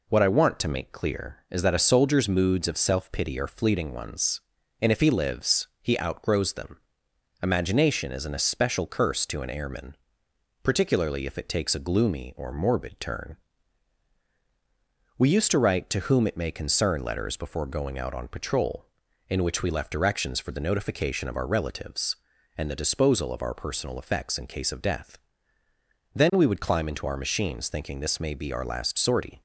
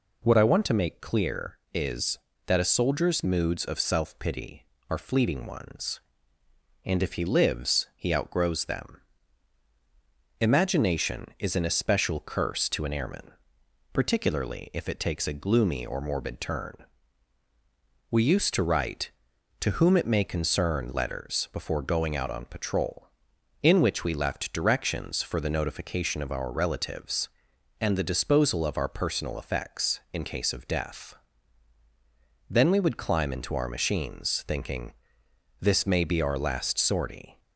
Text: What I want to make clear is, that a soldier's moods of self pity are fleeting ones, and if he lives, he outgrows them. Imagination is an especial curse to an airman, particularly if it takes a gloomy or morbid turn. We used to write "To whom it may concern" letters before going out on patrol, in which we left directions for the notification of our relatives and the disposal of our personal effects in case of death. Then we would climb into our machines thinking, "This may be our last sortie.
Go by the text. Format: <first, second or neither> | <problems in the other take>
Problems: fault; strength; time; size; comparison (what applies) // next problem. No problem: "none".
neither | none